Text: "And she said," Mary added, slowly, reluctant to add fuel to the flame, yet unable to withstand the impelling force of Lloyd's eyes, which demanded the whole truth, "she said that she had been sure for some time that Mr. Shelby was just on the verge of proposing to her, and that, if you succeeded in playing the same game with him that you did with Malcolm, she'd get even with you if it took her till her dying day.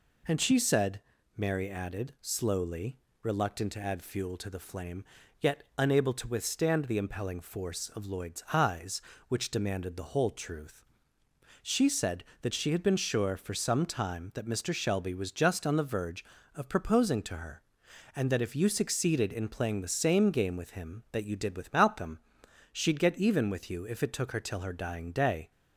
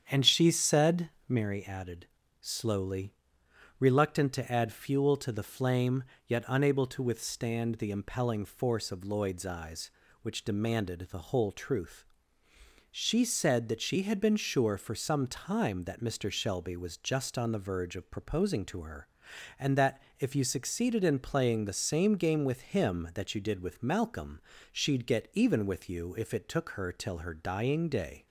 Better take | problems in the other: first | starts louder than the rest; strong; until 1.5 s; 8.5 dB

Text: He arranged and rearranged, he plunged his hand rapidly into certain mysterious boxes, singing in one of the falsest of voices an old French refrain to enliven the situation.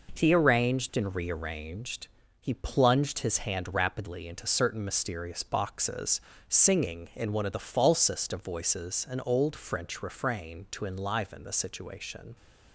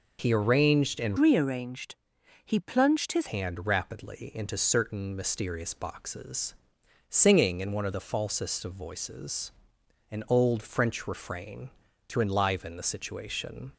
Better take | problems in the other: first | changes voice from "rearranged" to "his"; from 1.1 to 3.2 s; 2.1 s long // pauses between "voices" and "an"; noticeable; at 9.5 s; 0.62 s long

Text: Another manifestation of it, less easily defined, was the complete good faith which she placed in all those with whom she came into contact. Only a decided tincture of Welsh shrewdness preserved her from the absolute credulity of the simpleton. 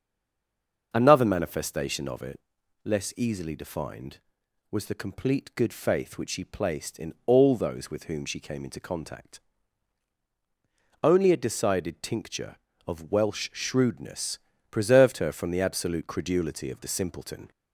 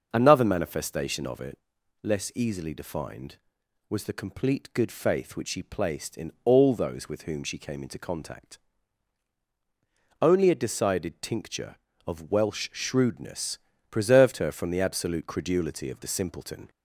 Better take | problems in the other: second | stays silent before the first word; slight; until 0.9 s; 0.9 s long // starts louder than the rest; until 1.9 s; 6 dB; noticeable in the second // pauses between "shrewdness" and "preserved"; slight; at 14.4 s; 0.32 s long; slight in the second

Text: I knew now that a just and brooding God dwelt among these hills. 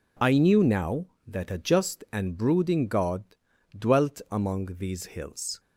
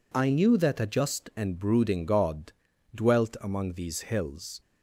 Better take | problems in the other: first | skips "now"; at 0.5 s // pauses between "God" and "dwelt"; at 2.5 s; 0.42 s long; also in the first

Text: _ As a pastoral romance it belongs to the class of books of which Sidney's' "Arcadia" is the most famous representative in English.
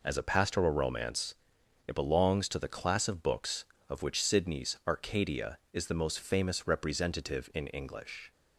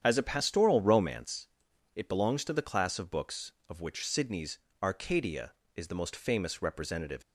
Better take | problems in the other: first | starts louder than the rest; strong; until 1.0 s; 9 dB // pauses between "romance" and "it"; noticeable; at 1.4 s; 0.48 s long; noticeable in the first // pauses between "Sidney's" and "Arcadia"; slight; at 4.5 s; 0.24 s long // stops before "in English"; at 7.2 s

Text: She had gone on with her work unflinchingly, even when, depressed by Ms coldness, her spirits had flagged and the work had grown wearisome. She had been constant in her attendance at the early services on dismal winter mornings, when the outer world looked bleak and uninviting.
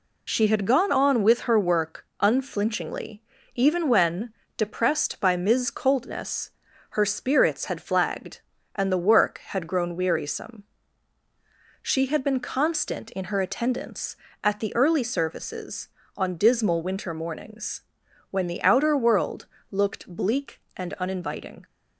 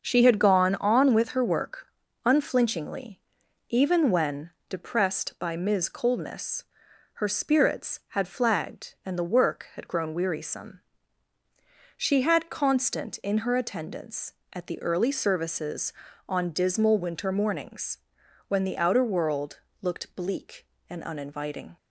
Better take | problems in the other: first | starts louder than the rest; until 1.0 s; 6.5 dB // pauses between "work" and "unflinchingly"; at 1.8 s; 0.38 s long; slight in the first // skips "been"; at 12.5 s // pauses between "world" and "looked"; slight; at 19.6 s; 0.22 s long; slight in the first

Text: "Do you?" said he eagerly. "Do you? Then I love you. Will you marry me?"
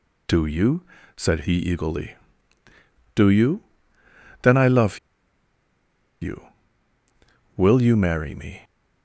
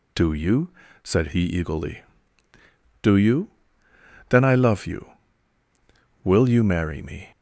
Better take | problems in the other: second | pauses between "love" and "you"; at 4.9 s; 1.2 s long

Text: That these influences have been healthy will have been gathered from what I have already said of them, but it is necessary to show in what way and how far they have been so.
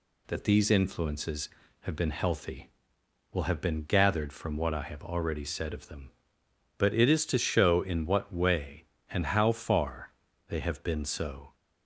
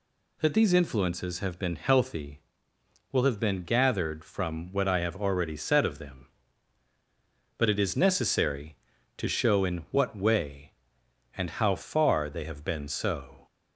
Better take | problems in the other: second | skips "necessary"; at 7.2 s // pauses between "far" and "they"; slight; at 10.1 s; 0.36 s long

